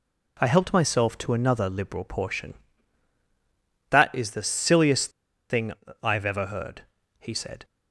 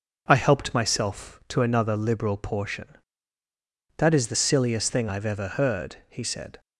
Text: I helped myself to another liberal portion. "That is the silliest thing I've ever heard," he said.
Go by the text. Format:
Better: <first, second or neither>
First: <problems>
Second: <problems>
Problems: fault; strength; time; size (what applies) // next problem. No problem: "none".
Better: second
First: pauses between "silliest" and "thing"; at 5.0 s; 0.40 s long // pauses between "thing" and "I've"; slight; at 5.7 s; 0.30 s long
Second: none